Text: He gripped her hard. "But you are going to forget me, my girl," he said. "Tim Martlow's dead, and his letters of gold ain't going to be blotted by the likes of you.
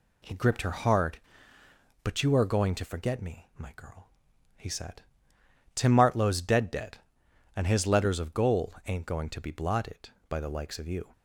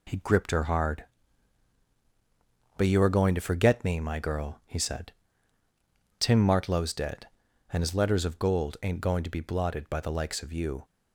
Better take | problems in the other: second | says "dead" twice; at 6.6 s

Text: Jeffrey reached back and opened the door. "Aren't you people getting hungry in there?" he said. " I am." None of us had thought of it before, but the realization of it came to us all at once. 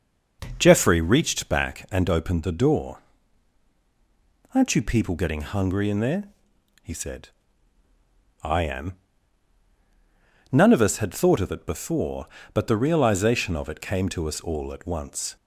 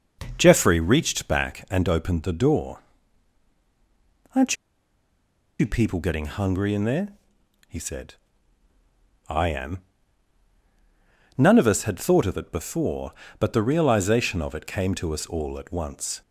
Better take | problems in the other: first | starts louder than the rest; until 1.3 s; 6 dB; noticeable in the first // pauses between "Aren't" and "you"; at 4.5 s; 1.0 s long

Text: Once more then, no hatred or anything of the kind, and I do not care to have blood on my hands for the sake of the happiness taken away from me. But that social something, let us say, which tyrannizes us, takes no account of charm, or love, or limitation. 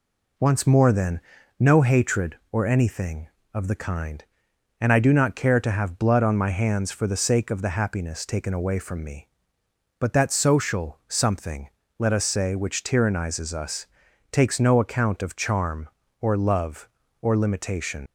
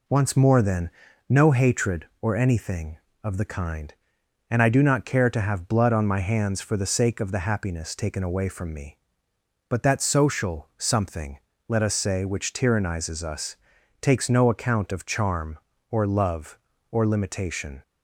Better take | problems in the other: second | leaves "limitation" unfinished; at 18.0 s; 60 ms

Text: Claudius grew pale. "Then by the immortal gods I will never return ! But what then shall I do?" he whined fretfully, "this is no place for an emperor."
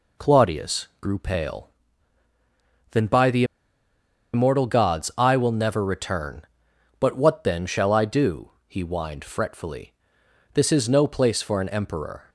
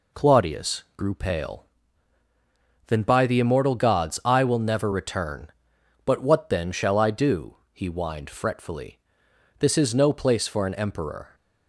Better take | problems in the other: second | pauses between "the" and "immortal"; noticeable; at 3.4 s; 0.89 s long

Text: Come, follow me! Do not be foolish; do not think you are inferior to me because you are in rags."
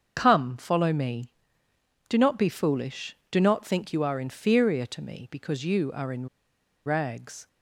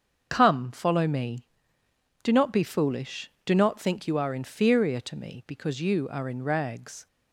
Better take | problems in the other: second | starts louder than the rest; until 1.1 s; 7 dB; also in the second // pauses between "in" and "rags"; noticeable; at 6.2 s; 0.59 s long

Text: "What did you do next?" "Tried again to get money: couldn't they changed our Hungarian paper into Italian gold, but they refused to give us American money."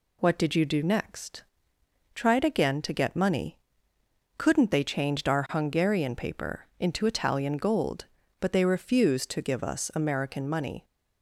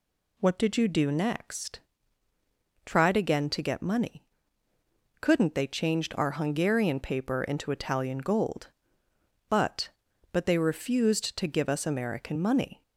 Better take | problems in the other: first | says "but" twice; at 10.3 s

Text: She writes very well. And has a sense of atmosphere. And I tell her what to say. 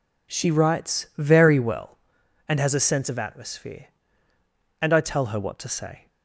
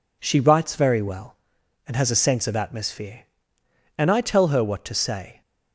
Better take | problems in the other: neither | none

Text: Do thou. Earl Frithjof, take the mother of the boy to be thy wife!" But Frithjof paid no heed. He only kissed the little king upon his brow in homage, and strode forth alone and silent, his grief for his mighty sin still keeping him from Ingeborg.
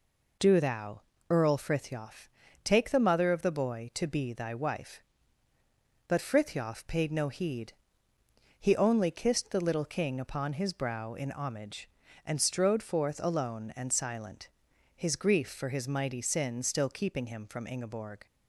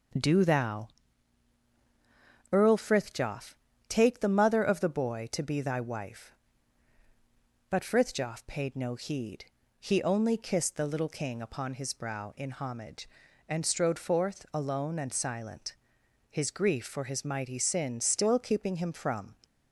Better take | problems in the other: first | starts louder than the rest; until 2.8 s; 6.5 dB // stops before "Ingeborg"; at 19.4 s

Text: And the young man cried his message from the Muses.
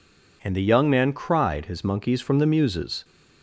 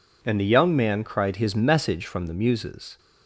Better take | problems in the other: second | says "monkeys" for "message"; at 1.8 s

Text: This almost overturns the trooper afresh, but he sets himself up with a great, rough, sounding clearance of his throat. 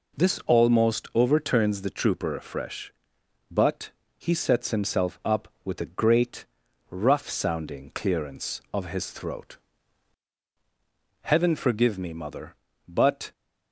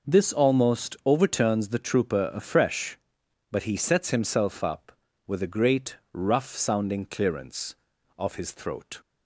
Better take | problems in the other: second | pauses between "but" and "he"; slight; at 3.8 s; 0.28 s long // goes on to say "Heaven forgive me mother but"; strong; from 11.2 s on; 2.1 s long

